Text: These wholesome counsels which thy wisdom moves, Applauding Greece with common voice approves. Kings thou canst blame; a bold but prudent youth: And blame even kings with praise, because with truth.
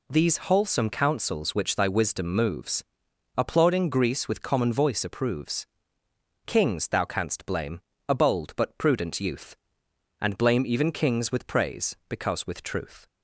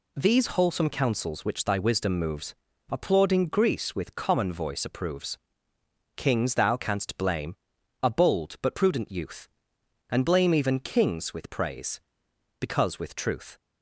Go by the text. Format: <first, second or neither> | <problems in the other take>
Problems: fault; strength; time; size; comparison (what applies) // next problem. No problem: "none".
neither | none